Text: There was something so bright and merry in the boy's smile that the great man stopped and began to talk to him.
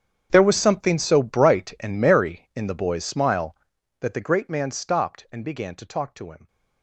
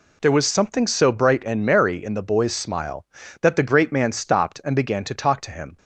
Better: second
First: gets quieter; strong; throughout; 20 dB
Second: none

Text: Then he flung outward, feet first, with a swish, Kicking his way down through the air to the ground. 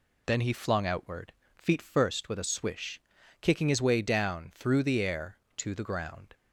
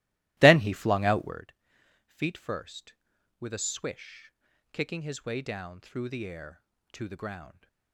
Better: first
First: none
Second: starts louder than the rest; strong; until 1.4 s; 17 dB

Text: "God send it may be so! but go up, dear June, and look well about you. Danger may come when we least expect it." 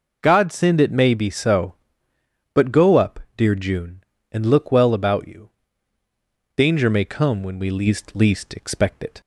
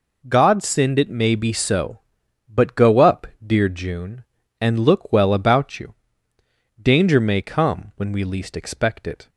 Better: second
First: says "least" twice; at 8.1 s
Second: none

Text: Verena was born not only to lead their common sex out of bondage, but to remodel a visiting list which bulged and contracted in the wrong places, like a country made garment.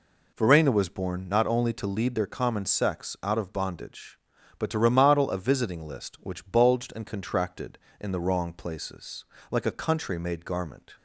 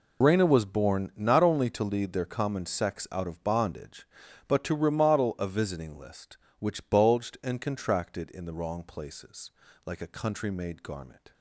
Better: first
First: none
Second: loses the start of "Verena"; at 0.2 s; 125 ms

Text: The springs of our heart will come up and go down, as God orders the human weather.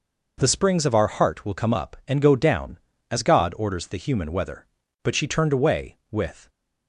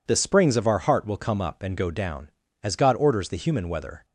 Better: second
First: goes on to say "But she turned away with"; from 5.0 s on; 1.4 s long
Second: none

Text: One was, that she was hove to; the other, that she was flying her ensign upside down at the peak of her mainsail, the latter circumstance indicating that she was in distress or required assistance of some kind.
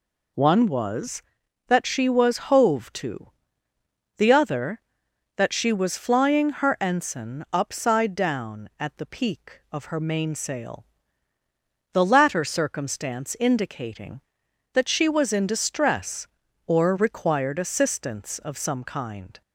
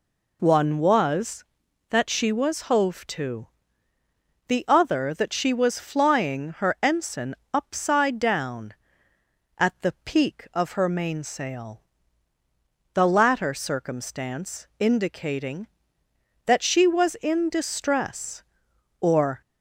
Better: first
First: none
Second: pauses between "ensign" and "upside"; slight; at 7.3 s; 0.18 s long // stops before "required assistance of some kind"; at 19.4 s

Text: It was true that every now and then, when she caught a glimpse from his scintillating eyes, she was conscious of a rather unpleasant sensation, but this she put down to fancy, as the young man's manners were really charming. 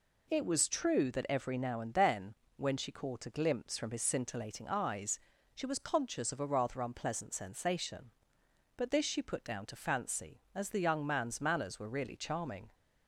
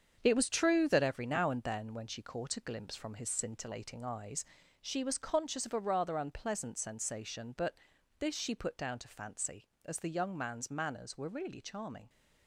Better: first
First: none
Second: gets quieter; strong; throughout; 8 dB // pauses between "but" and "this"; at 7.7 s; 0.44 s long

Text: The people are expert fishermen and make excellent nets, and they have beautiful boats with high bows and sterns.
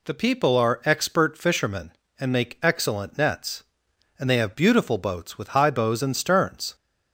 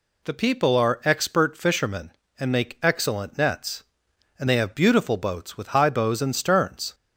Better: neither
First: none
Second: none

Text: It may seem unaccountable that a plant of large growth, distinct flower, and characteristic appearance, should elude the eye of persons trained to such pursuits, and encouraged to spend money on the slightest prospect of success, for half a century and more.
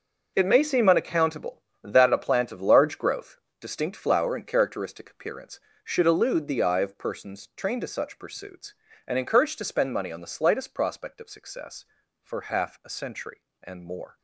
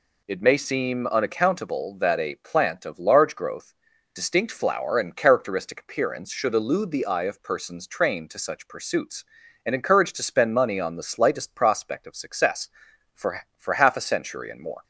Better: first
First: none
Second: says "for" twice; at 13.5 s

